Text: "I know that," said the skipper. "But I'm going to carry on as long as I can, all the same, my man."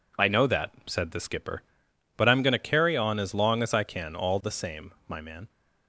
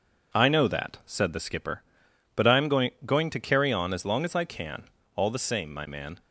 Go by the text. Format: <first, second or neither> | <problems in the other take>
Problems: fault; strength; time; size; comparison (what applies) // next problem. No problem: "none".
first | says "going" twice; at 3.0 s